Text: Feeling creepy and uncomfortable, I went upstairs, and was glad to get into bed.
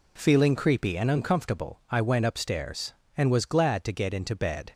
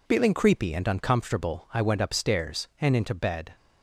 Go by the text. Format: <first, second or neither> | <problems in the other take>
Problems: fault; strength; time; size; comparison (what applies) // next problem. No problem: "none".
first | skips "was glad to get"; at 2.9 s